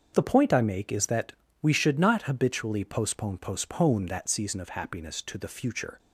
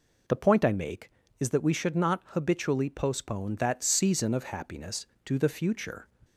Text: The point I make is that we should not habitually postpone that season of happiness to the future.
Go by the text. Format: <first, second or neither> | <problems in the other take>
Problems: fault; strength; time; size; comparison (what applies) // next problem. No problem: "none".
second | starts louder than the rest; until 1.1 s; 6.5 dB // pauses between "that" and "we"; slight; at 1.3 s; 0.28 s long // says "postpone" twice; at 3.3 s